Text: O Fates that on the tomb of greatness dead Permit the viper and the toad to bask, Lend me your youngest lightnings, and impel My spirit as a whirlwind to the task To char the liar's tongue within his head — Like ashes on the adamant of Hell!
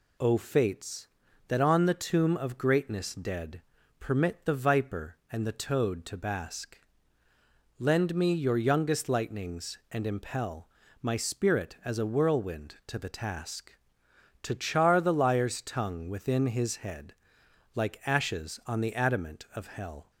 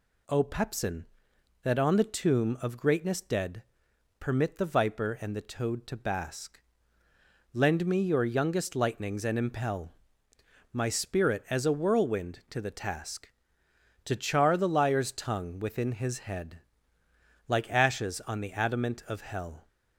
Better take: first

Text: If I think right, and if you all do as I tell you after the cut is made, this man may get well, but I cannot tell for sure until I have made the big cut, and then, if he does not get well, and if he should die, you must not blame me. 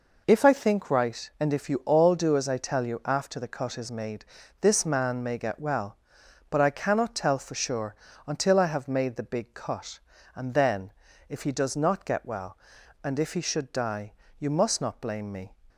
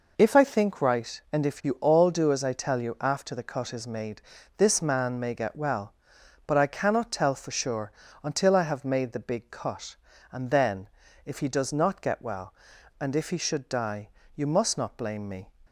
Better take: neither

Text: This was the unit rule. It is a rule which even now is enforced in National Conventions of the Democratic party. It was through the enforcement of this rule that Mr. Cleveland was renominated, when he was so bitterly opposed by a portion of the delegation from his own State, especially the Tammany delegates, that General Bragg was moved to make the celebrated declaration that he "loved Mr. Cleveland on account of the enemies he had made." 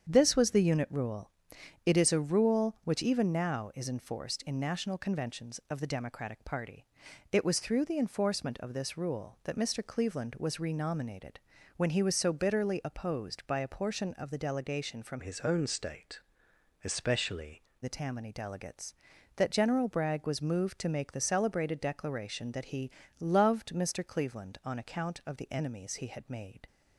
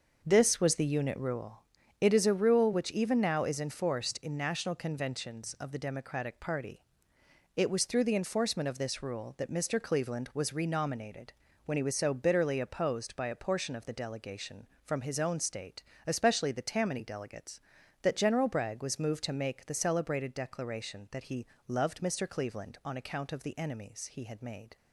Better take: second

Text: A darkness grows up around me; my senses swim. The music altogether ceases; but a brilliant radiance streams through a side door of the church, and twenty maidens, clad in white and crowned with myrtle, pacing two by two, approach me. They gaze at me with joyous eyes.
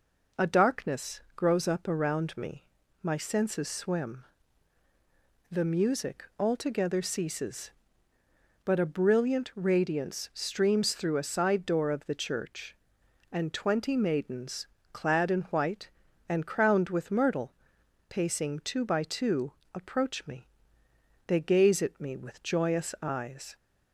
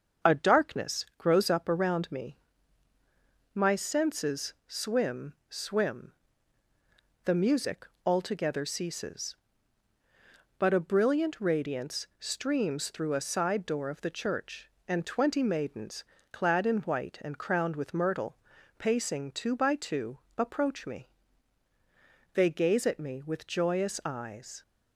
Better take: first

